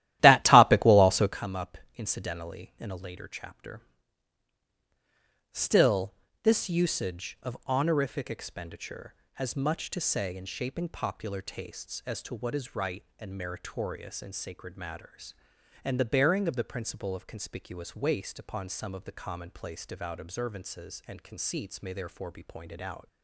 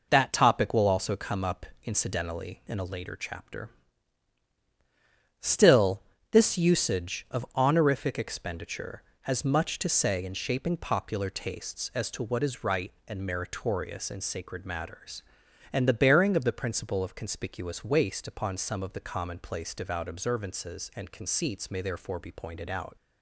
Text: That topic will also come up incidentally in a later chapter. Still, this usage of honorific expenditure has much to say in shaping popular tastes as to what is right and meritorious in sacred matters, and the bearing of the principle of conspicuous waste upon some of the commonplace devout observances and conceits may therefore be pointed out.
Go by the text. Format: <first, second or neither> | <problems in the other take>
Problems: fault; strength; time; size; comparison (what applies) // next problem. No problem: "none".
second | starts louder than the rest; strong; until 1.4 s; 14 dB // pauses between "up" and "incidentally"; slight; at 1.7 s; 0.18 s long; slight in the second